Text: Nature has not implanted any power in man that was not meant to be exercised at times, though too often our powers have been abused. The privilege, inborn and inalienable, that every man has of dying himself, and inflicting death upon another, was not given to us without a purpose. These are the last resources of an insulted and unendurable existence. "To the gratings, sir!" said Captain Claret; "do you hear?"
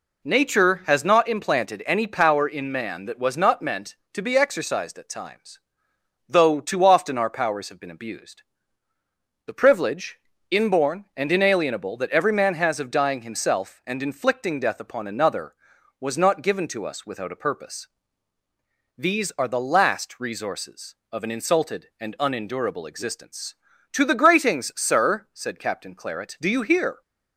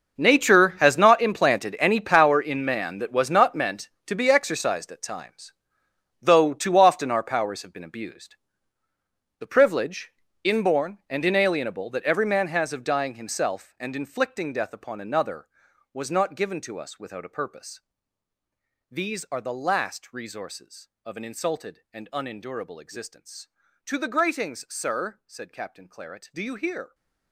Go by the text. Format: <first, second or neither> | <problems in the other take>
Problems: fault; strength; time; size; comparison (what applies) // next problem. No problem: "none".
first | gets quieter; strong; throughout; 16 dB